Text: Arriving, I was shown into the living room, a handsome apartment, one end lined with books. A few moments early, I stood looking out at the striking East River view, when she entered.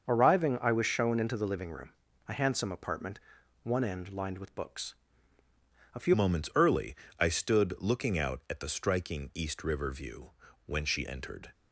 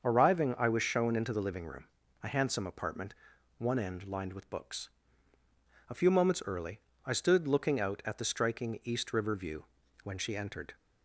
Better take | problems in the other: second | starts louder than the rest; until 1.1 s; 6.5 dB; also in the second // changes voice at "moments"; from 6.1 s on; 5.4 s long

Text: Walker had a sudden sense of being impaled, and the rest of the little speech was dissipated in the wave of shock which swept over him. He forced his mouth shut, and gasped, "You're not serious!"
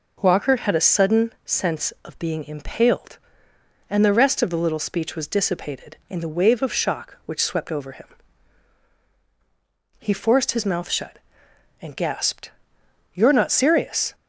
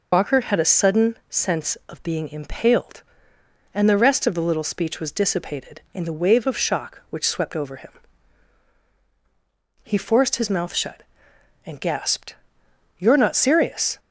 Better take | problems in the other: first | loses the start of "Walker"; at 0.1 s; 105 ms

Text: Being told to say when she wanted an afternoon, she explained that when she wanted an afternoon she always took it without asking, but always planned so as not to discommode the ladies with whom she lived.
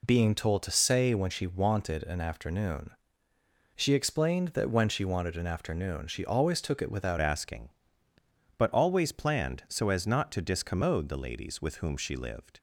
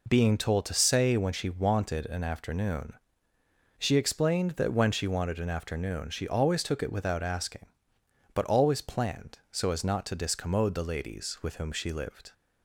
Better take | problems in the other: second | changes voice at "asking"; from 7.2 s on; 5.3 s long

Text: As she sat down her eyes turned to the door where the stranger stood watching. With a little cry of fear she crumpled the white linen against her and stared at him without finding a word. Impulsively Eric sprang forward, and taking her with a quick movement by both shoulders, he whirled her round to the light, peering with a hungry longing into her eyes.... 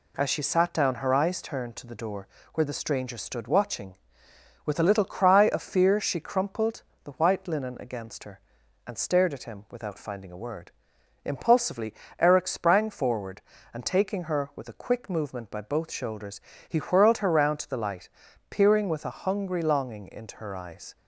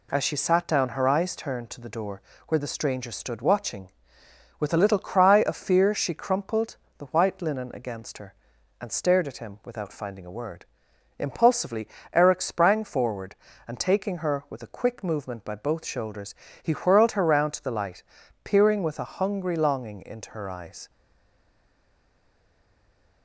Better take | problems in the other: first | pauses between "door" and "where"; slight; at 2.2 s; 0.26 s long; slight in the first // pauses between "crumpled" and "the"; slight; at 6.7 s; 0.20 s long; slight in the first // pauses between "Impulsively" and "Eric"; slight; at 11.8 s; 0.24 s long; slight in the first // stays silent after the last word; from 20.8 s on; 2.4 s long

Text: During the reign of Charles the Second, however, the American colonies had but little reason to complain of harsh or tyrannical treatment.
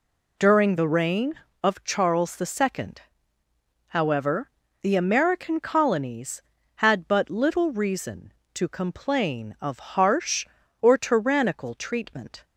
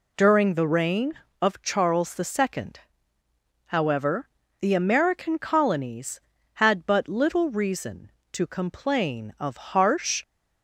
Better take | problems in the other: first | stops before "or tyrannical treatment"; at 10.2 s

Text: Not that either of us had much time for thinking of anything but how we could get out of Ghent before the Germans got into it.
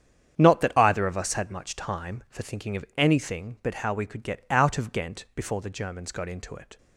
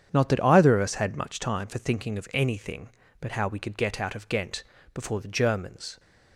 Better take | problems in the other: first | starts louder than the rest; strong; until 1.1 s; 8.5 dB; strong in the first // pauses between "Ghent" and "before"; slight; at 4.6 s; 0.30 s long // stops before "got into it"; at 5.9 s

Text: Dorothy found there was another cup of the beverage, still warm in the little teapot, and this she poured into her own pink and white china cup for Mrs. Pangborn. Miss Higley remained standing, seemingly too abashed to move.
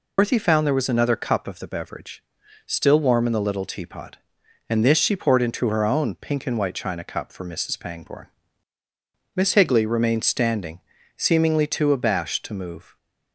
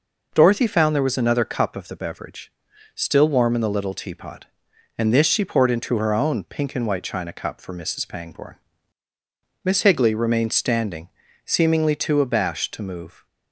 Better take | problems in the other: second | loses the start of "Dorothy"; at 0.1 s; 135 ms

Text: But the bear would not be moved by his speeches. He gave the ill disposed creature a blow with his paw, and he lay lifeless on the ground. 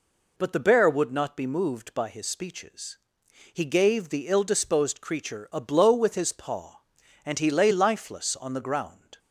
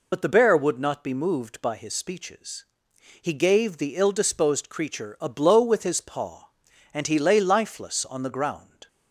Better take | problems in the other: first | loses the start of "But"; at 0.1 s; 50 ms

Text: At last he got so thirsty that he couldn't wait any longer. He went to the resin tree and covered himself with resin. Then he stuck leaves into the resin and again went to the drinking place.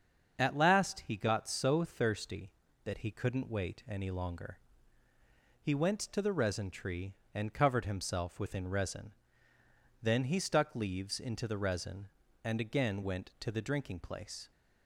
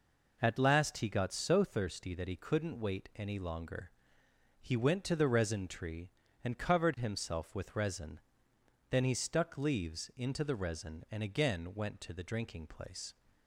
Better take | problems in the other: second | starts louder than the rest; until 1.4 s; 7 dB // says "within" for "with"; at 8.4 s

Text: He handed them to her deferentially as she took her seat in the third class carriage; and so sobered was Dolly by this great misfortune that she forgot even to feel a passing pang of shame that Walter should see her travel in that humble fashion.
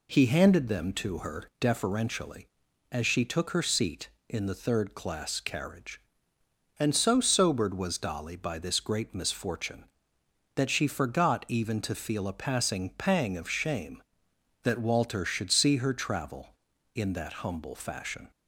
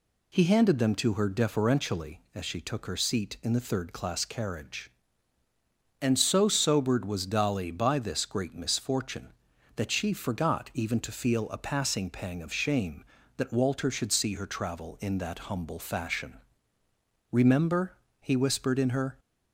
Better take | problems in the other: first | goes on to say "Remember he whispered in her"; strong; from 17.3 s on; 1.8 s long

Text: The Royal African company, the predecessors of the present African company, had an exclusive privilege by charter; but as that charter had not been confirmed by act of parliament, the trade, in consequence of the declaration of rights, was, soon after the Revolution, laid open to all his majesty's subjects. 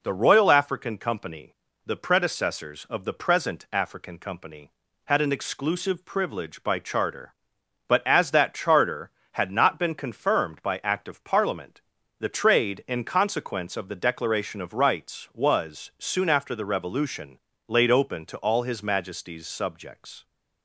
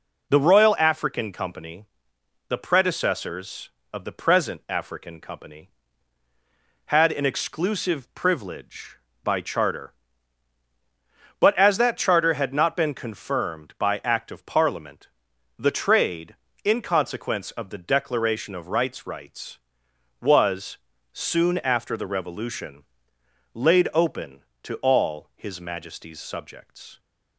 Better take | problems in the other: first | says "rights" twice; at 19.0 s

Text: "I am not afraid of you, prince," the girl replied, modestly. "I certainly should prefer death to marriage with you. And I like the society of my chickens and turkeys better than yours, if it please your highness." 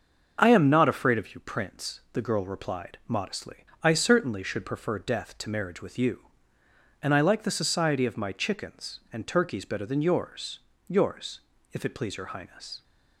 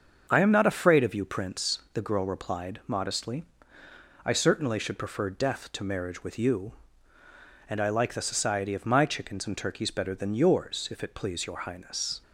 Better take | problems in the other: second | starts louder than the rest; until 1.4 s; 6 dB; also in the second // says "yours" twice; at 10.8 s

